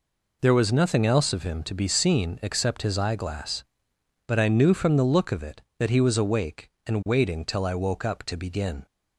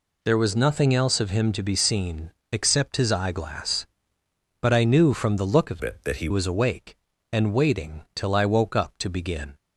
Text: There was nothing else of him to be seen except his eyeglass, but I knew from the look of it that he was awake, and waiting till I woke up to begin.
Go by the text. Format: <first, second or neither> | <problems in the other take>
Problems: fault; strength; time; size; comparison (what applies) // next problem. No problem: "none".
first | pauses between "seen" and "except"; slight; at 2.2 s; 0.22 s long // changes voice from "it" to "he"; from 5.8 to 6.2 s; 0.4 s long